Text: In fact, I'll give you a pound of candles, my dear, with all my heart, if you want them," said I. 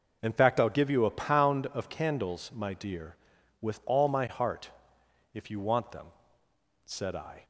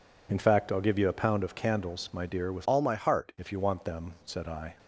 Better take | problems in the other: first | changes voice from "all" to "heart"; from 2.6 to 3.3 s; 0.7 s long

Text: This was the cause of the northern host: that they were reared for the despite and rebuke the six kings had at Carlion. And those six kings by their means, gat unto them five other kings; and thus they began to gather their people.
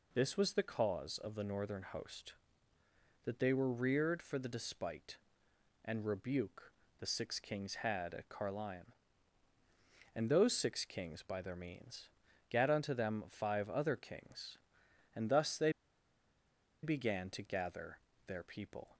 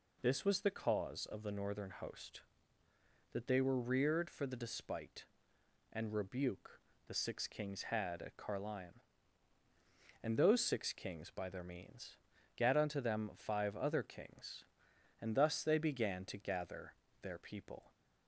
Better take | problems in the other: second | pauses between "rebuke" and "the"; slight; at 6.7 s; 0.26 s long; slight in the second // pauses between "they" and "began"; at 15.7 s; 1.1 s long // pauses between "gather" and "their"; slight; at 17.9 s; 0.26 s long; slight in the second

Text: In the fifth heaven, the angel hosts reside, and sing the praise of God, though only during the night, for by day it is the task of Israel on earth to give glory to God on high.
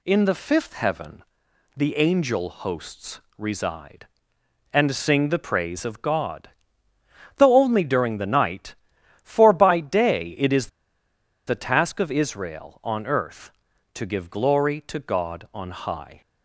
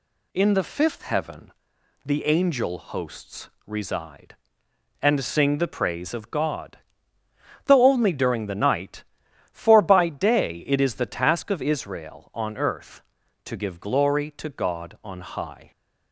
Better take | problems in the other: second | pauses between "hosts" and "reside"; slight; at 3.1 s; 0.18 s long; slight in the second // pauses between "is" and "the"; noticeable; at 10.6 s; 0.79 s long

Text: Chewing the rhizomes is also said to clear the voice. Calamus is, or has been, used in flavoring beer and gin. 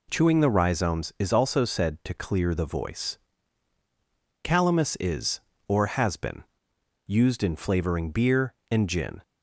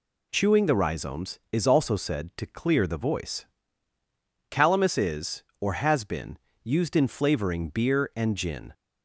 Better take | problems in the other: neither | none

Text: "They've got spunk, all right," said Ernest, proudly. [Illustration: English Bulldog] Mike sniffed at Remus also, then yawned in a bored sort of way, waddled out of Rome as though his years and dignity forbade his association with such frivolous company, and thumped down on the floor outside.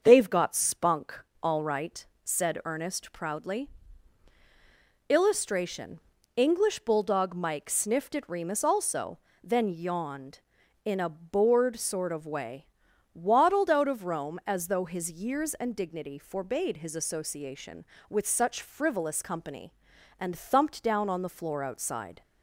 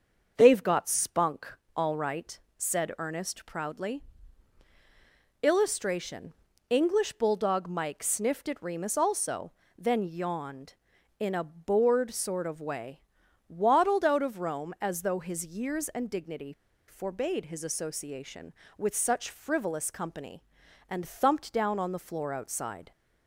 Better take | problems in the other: first | starts louder than the rest; until 1.4 s; 6.5 dB; also in the first // pauses between "dignity" and "forbade"; at 16.5 s; 0.36 s long

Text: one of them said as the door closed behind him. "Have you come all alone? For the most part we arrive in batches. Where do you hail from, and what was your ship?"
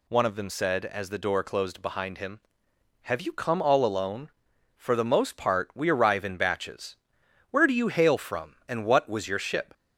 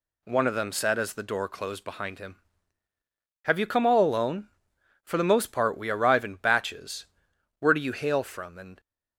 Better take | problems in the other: first | stops before "what was your ship"; at 8.7 s

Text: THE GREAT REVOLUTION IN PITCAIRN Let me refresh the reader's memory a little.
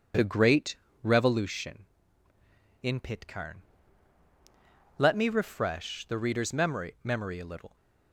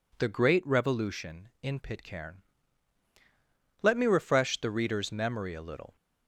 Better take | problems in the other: second | pauses between "GREAT" and "REVOLUTION"; slight; at 0.7 s; 0.26 s long // pauses between "PITCAIRN" and "Let"; strong; at 3.5 s; 1.3 s long; strong in the second // says "memory" twice; at 7.0 s

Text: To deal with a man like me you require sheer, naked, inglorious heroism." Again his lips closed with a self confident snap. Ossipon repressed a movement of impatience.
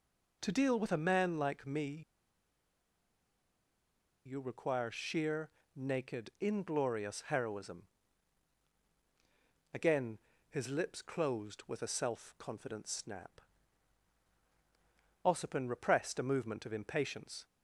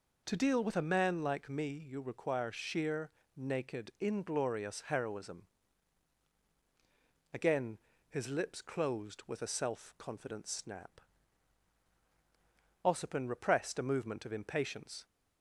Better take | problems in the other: second | pauses between "me" and "you"; strong; at 2.0 s; 2.2 s long // pauses between "Again" and "his"; slight; at 10.1 s; 0.32 s long; slight in the second

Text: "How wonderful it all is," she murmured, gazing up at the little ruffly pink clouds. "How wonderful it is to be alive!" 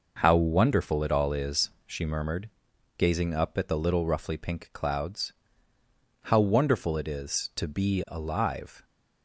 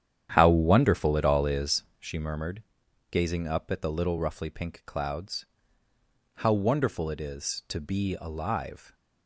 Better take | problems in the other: first | starts louder than the rest; strong; until 1.8 s; 10 dB

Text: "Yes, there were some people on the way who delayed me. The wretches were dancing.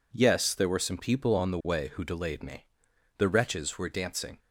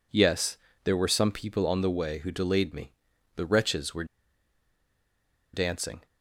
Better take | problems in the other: first | pauses between "were" and "dancing"; strong; at 4.0 s; 1.4 s long

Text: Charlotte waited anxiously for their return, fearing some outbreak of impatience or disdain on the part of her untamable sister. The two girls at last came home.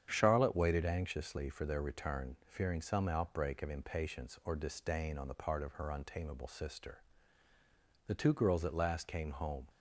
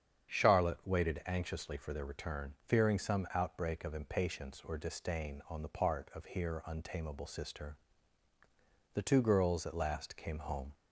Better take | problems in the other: first | starts louder than the rest; strong; until 1.4 s; 8 dB; strong in the first // says "here" for "her"; at 6.2 s

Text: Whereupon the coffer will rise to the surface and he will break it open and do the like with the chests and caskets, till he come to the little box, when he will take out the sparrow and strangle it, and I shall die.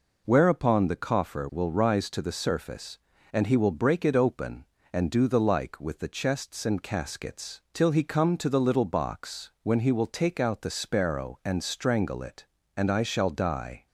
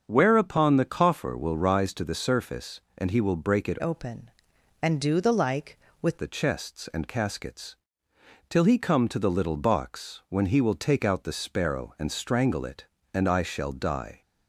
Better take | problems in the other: first | starts louder than the rest; until 1.0 s; 6.5 dB // changes voice from "open" to "with"; from 3.8 to 6.1 s; 2.3 s long

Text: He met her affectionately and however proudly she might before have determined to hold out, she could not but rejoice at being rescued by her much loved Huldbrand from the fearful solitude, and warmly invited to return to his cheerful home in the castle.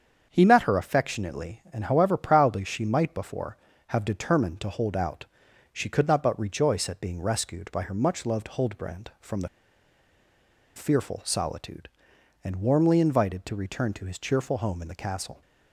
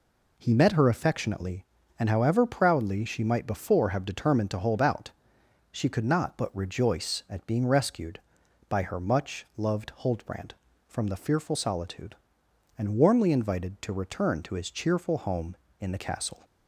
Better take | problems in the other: second | starts louder than the rest; strong; until 1.3 s; 7 dB // pauses between "the" and "fearful"; strong; at 9.4 s; 1.2 s long

